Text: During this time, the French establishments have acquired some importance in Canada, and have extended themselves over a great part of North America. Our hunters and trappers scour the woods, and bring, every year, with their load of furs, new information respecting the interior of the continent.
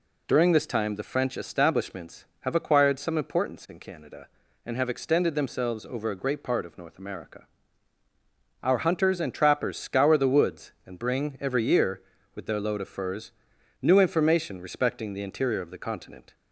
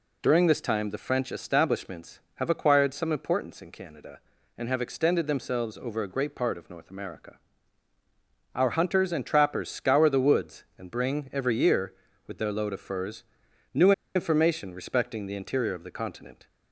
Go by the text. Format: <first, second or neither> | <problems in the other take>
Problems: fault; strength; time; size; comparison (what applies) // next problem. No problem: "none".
first | pauses between "new" and "information"; slight; at 13.9 s; 0.23 s long